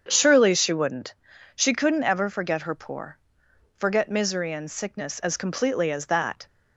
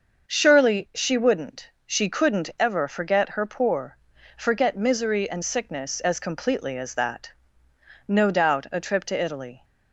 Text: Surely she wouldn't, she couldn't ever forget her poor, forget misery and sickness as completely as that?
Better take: first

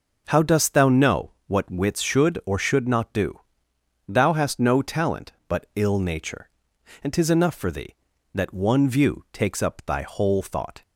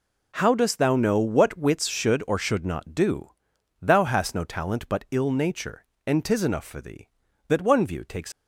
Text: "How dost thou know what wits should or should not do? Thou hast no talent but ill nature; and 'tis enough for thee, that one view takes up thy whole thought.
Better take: first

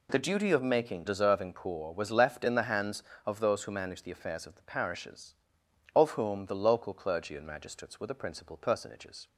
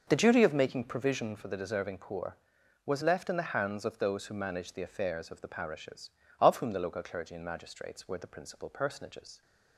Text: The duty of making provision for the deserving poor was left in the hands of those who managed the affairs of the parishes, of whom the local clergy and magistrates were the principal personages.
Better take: second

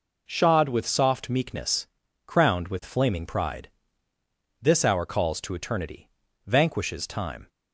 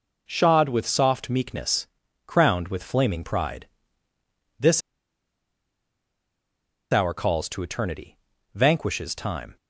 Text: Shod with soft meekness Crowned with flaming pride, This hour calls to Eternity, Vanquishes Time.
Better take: first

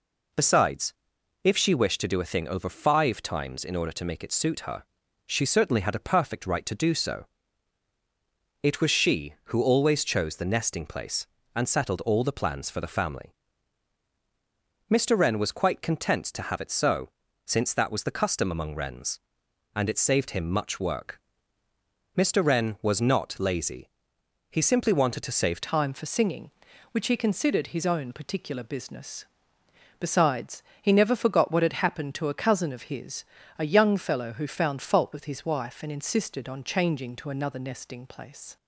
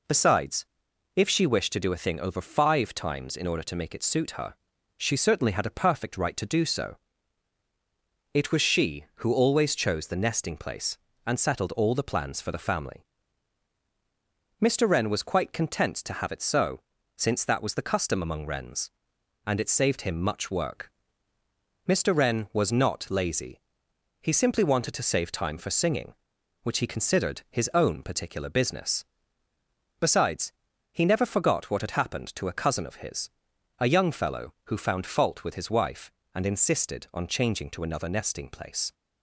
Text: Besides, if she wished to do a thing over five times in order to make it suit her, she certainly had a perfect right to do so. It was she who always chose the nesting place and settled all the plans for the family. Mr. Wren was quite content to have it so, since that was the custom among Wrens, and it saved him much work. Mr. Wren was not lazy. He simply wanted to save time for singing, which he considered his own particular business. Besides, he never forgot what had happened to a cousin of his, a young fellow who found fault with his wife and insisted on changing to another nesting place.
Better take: second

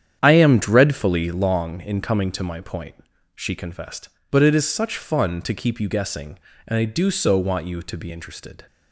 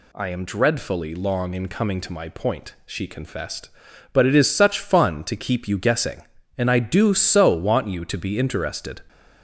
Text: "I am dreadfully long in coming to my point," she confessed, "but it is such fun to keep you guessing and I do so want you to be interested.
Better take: second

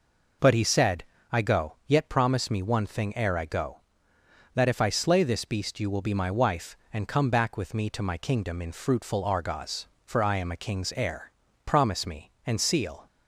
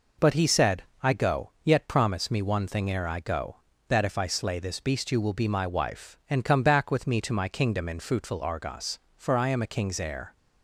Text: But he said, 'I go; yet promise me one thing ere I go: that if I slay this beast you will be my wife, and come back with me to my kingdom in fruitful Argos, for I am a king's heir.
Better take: second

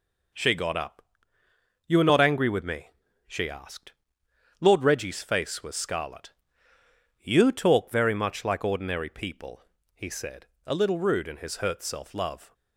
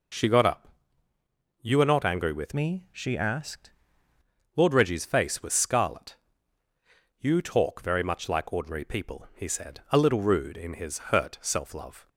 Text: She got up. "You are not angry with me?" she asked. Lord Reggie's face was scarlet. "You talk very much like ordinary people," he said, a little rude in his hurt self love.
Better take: first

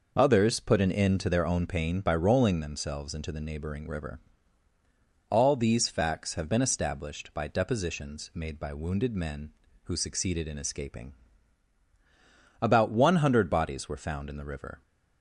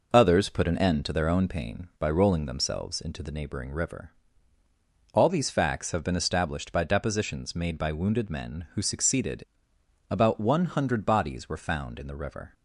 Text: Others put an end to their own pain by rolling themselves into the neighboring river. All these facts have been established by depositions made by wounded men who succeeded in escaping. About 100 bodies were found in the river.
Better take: first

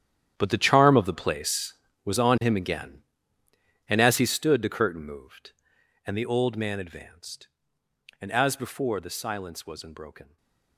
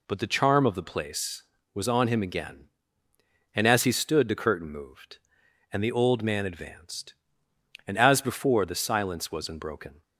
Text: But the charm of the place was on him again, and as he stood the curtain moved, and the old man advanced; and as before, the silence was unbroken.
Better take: second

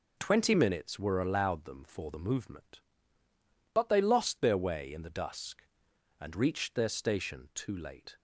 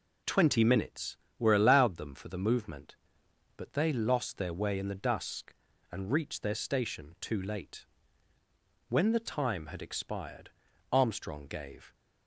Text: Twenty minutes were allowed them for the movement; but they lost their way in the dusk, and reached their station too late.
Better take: first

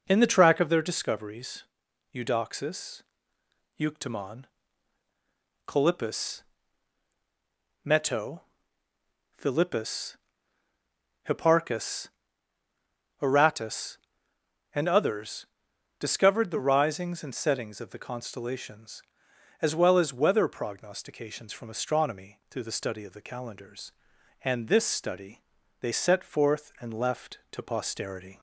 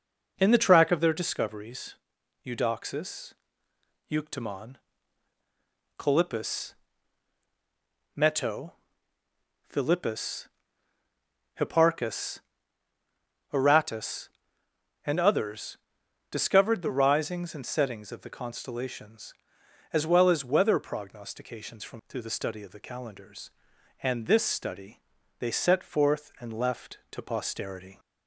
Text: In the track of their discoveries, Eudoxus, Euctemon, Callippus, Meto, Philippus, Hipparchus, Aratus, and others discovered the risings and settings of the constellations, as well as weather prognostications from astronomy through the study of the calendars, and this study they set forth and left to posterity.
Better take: first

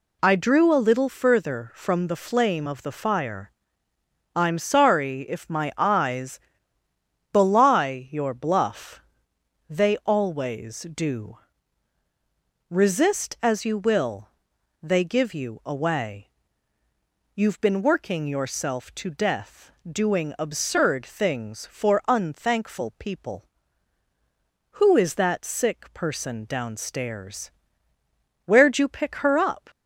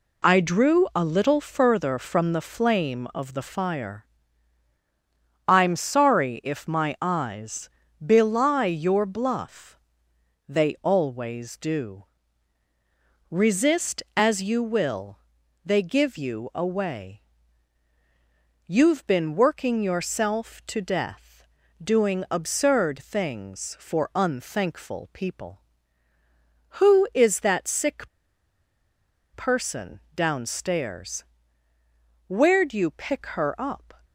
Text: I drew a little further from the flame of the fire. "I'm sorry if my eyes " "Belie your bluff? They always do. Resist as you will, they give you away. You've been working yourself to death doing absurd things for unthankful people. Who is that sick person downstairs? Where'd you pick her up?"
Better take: first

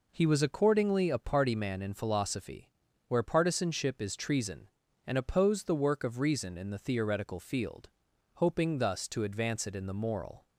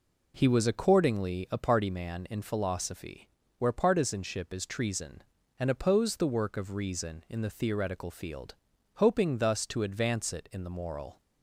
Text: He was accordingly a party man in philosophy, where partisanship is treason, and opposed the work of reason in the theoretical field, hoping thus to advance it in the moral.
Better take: neither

